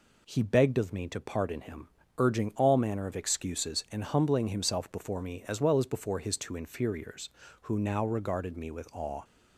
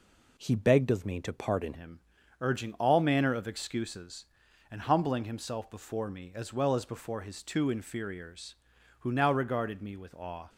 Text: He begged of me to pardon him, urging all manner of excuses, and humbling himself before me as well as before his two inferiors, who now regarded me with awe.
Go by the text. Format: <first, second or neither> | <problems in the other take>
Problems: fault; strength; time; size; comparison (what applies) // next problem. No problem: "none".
first | changes voice at "him"; from 1.7 s on; 8.7 s long